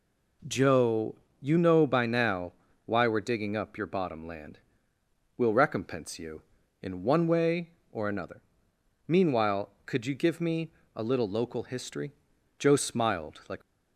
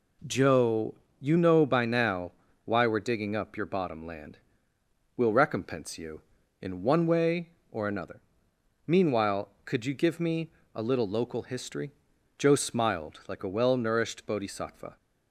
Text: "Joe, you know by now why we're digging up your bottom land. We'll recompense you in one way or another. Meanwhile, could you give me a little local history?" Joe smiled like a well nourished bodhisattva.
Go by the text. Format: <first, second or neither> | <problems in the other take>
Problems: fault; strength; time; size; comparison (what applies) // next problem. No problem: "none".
second | pauses between "now" and "why"; slight; at 2.5 s; 0.32 s long; slight in the second // pauses between "me" and "a"; slight; at 10.7 s; 0.24 s long; slight in the second // stops before "a well nourished bodhisattva"; at 13.6 s